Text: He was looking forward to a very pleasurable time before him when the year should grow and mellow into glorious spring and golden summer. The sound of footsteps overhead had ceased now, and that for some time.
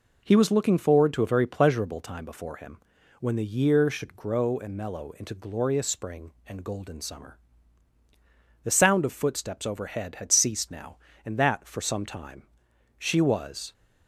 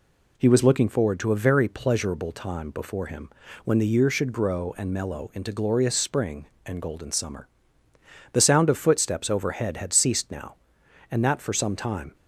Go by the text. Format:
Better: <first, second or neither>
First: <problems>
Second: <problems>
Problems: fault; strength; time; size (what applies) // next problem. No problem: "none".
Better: second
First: pauses between "him" and "when"; at 2.7 s; 0.40 s long // goes on to say "She was"; noticeable; from 12.9 s on; 0.76 s long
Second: pauses between "him" and "when"; slight; at 3.2 s; 0.34 s long